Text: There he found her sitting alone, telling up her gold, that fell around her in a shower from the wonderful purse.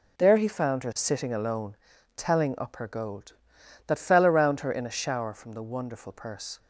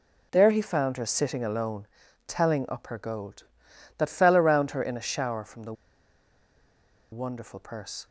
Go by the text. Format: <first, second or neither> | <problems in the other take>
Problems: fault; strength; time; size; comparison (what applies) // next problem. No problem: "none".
first | pauses between "the" and "wonderful"; strong; at 5.7 s; 1.3 s long